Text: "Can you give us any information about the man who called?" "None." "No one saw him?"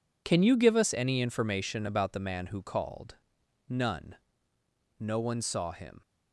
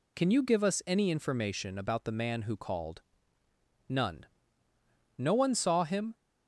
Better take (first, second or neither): second